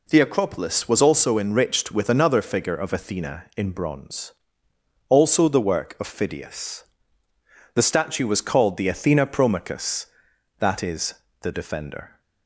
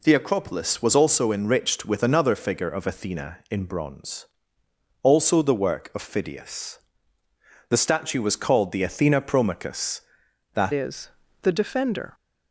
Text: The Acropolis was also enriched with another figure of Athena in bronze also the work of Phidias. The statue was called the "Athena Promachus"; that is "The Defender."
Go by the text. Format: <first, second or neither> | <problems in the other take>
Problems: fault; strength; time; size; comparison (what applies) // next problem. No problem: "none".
first | pauses between "bronze" and "also"; noticeable; at 4.2 s; 0.78 s long; noticeable in the first // changes voice at "is"; from 10.7 s on; 1.4 s long // pauses between "is" and "The"; slight; at 11.1 s; 0.32 s long; slight in the first